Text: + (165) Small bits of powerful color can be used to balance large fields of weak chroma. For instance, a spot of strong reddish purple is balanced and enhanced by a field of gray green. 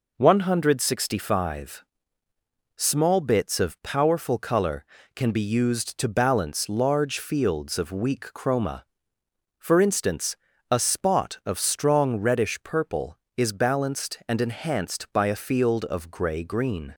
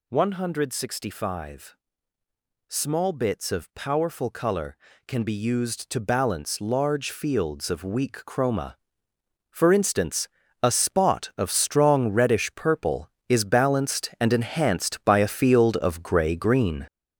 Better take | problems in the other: first | gets louder; strong; throughout; 7.5 dB

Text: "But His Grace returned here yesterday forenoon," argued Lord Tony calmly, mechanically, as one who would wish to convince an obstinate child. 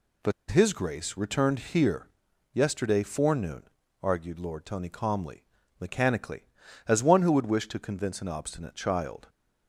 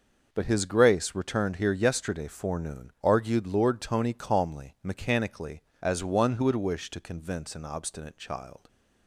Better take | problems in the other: second | pauses between "But" and "His"; slight; at 0.3 s; 0.18 s long // pauses between "here" and "yesterday"; at 2.0 s; 0.44 s long

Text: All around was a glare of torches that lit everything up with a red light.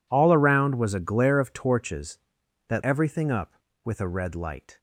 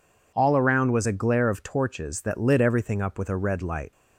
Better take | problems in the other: second | skips "lit"; at 2.8 s

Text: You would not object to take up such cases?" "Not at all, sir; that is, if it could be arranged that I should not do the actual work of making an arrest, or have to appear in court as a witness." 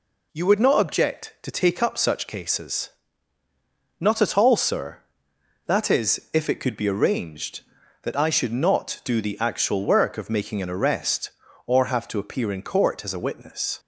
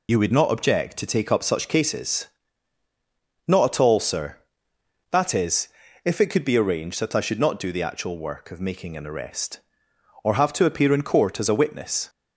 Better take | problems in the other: first | loses the start of "You"; at 0.0 s; 30 ms

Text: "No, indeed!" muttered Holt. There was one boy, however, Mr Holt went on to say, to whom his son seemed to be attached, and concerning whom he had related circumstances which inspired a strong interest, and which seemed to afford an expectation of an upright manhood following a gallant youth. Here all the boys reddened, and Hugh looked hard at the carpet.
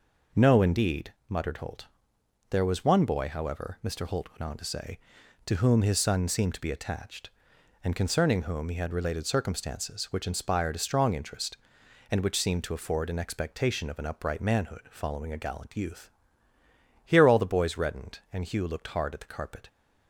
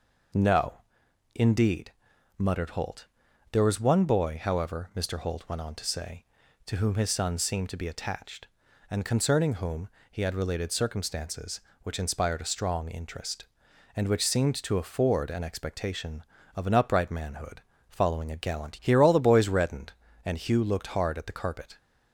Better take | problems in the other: first | pauses between "whom" and "he"; slight; at 9.9 s; 0.20 s long // pauses between "manhood" and "following"; slight; at 17.6 s; 0.30 s long // skips "youth"; at 18.7 s

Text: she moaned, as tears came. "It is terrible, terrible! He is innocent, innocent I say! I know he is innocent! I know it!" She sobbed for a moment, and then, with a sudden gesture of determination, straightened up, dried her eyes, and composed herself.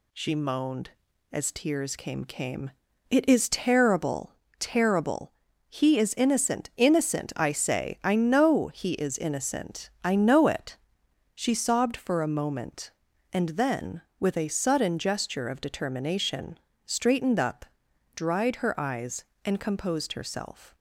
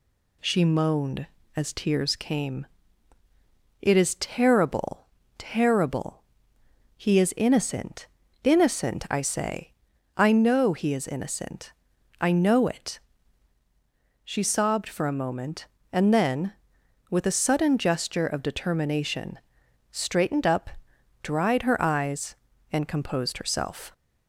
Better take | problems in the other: second | says "came" twice; at 2.2 s

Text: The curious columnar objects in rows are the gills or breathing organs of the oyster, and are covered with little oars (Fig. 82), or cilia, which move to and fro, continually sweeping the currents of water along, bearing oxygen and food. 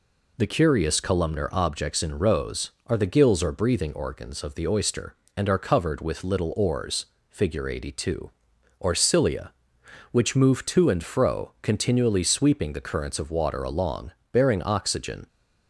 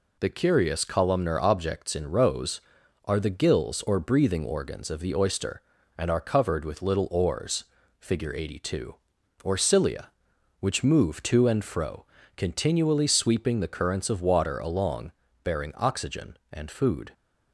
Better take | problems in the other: second | stops before "and food"; at 15.2 s

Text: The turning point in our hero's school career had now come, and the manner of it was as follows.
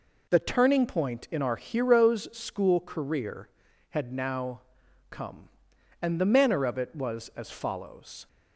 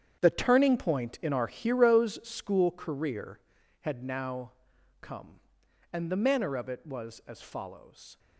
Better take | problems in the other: first | gets quieter; strong; throughout; 13.5 dB // pauses between "now" and "come"; noticeable; at 4.5 s; 0.50 s long; noticeable in the first

